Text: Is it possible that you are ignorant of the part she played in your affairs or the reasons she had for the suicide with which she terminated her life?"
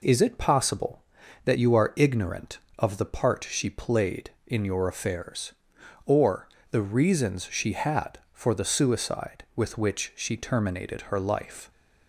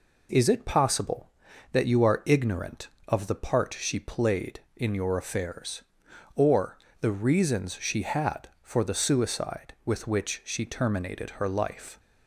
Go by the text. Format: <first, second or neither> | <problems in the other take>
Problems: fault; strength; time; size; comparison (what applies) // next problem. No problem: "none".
neither | pauses between "or" and "the"; slight; the same in both